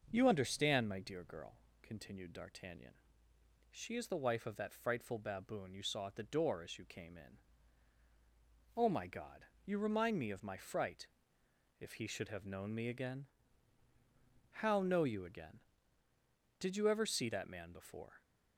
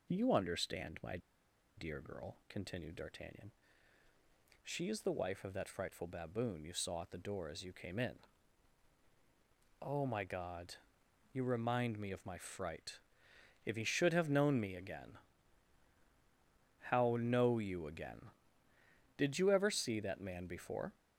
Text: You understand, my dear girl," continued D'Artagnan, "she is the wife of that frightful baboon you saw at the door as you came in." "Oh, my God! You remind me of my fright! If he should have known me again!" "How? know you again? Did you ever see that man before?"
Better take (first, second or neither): first